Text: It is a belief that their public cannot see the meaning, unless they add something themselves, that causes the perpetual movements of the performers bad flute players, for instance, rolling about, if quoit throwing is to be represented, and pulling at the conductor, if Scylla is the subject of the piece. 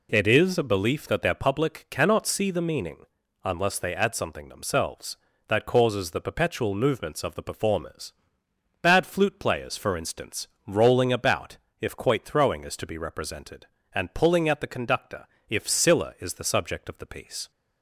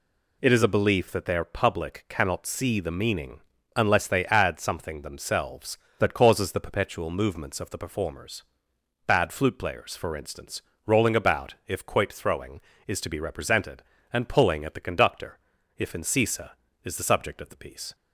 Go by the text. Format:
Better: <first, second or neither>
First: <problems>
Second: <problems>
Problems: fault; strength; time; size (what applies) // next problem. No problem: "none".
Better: first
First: pauses between "performers" and "bad"; noticeable; at 8.1 s; 0.70 s long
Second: pauses between "performers" and "bad"; noticeable; at 8.4 s; 0.62 s long // says "Incisa" for "Scylla"; at 15.9 s